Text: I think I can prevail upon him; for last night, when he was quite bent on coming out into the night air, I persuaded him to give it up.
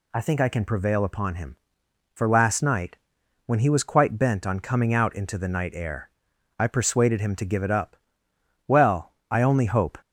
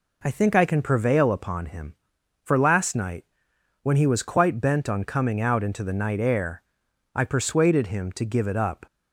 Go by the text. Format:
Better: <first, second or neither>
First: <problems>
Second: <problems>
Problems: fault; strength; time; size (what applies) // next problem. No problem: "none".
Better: second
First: goes on to say "Well I only hope"; from 8.6 s on; 1.3 s long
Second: none